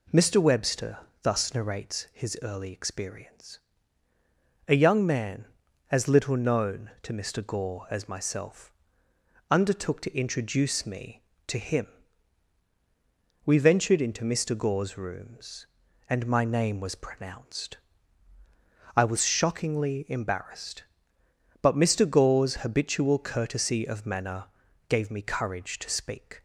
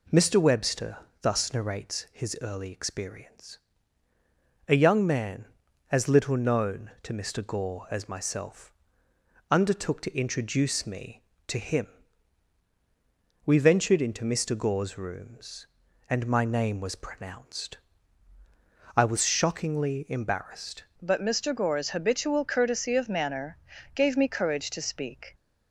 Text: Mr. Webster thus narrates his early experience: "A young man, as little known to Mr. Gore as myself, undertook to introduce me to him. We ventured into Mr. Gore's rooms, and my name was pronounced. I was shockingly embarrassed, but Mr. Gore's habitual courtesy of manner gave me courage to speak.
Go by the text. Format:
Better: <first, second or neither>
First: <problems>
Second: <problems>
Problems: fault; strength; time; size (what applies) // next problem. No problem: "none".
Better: first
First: pauses between "Webster" and "thus"; slight; at 0.9 s; 0.24 s long // pauses between "manner" and "gave"; at 24.4 s; 0.44 s long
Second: pauses between "Webster" and "thus"; slight; at 0.9 s; 0.24 s long // changes voice at "but"; from 21.0 s on; 4.3 s long // pauses between "manner" and "gave"; at 23.5 s; 0.40 s long